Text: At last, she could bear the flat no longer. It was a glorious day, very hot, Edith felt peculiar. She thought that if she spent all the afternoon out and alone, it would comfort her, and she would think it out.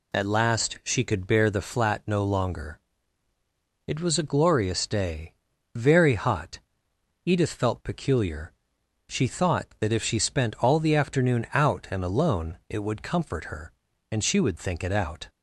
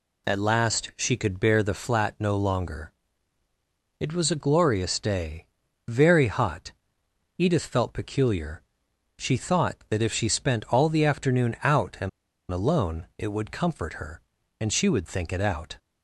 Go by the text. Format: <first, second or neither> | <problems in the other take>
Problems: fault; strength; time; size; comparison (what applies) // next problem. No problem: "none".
first | pauses between "and" and "alone"; at 12.0 s; 0.42 s long